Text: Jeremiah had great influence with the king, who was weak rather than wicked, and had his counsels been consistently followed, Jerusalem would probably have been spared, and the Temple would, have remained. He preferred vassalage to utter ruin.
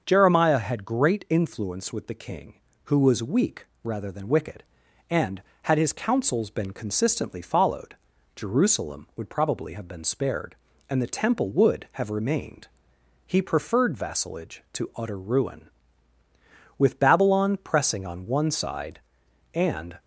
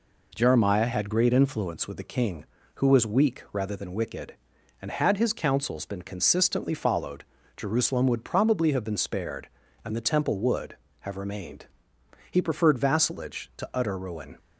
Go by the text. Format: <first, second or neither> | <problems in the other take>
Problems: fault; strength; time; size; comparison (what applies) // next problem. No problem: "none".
second | starts louder than the rest; until 1.0 s; 6.5 dB // pauses between "weak" and "rather"; slight; at 3.6 s; 0.18 s long // goes on to say "With Babylon pressing on one side and"; strong; from 16.7 s on; 3.2 s long